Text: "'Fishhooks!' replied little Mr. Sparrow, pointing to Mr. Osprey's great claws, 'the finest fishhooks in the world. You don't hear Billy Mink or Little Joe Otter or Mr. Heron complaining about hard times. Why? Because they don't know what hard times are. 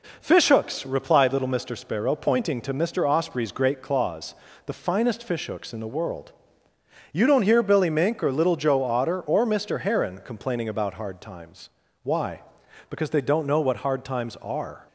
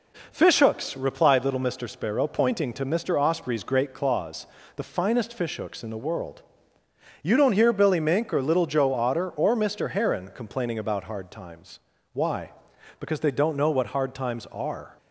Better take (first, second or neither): neither